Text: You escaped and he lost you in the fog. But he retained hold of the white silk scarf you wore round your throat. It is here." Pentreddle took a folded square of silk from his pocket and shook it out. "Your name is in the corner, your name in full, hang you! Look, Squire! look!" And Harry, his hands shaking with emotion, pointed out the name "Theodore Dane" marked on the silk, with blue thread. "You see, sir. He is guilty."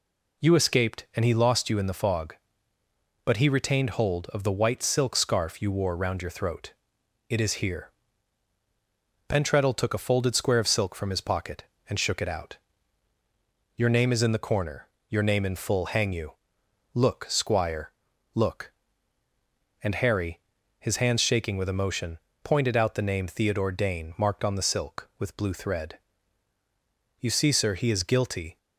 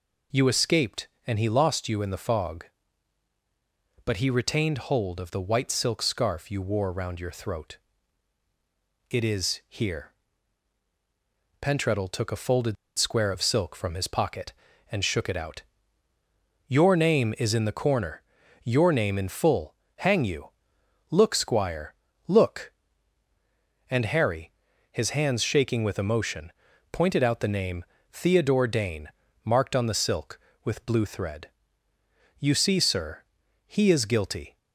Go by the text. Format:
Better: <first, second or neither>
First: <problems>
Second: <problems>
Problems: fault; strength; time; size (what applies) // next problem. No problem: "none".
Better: first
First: none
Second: pauses between "folded" and "square"; slight; at 12.7 s; 0.23 s long // pauses between "name" and "Theodore"; slight; at 27.8 s; 0.28 s long // pauses between "Dane" and "marked"; slight; at 29.0 s; 0.34 s long